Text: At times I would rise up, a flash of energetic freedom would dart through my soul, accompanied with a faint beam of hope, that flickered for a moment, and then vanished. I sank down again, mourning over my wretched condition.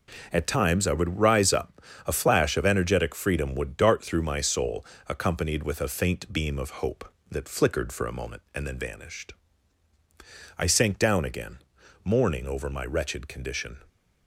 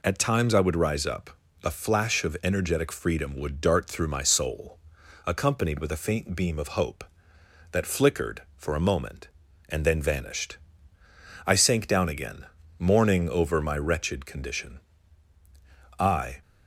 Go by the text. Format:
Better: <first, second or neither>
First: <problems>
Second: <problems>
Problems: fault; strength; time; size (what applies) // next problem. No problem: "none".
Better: first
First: none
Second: goes on to say "I"; slight; from 15.9 s on; 0.44 s long